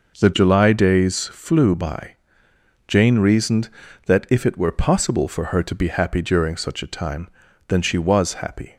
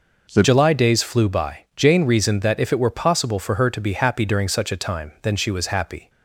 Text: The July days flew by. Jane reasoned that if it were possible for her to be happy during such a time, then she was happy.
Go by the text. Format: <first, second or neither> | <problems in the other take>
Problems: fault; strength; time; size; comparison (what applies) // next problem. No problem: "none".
first | changes voice at "July"; from 0.4 s on; 5.6 s long